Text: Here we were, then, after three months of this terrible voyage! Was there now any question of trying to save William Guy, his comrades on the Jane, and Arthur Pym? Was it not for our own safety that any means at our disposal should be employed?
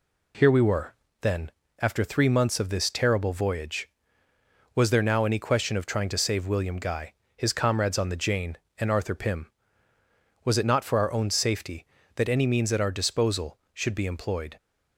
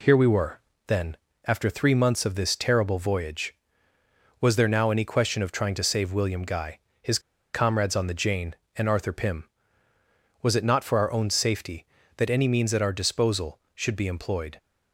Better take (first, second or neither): first